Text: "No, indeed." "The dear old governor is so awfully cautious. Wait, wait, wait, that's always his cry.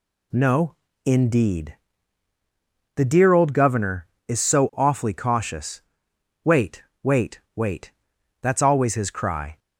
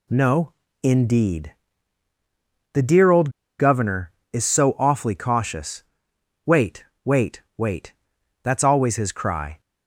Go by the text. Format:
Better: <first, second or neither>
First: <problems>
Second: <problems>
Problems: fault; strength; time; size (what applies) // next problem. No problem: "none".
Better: first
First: none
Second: pauses between "old" and "governor"; slight; at 3.2 s; 0.30 s long